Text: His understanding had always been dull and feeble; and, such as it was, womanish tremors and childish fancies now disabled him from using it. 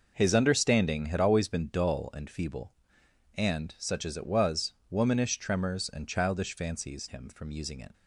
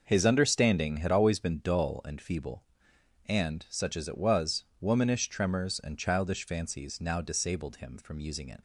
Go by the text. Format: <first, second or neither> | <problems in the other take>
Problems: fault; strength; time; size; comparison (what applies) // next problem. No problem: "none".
second | skips "now disabled"; at 7.0 s